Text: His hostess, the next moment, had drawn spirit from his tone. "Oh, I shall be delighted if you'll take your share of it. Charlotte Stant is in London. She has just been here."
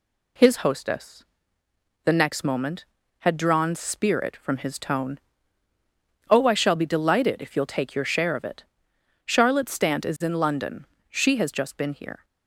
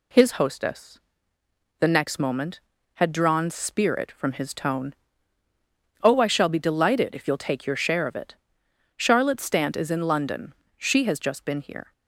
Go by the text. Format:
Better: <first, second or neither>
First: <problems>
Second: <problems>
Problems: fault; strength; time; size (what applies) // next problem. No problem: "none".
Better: neither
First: none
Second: none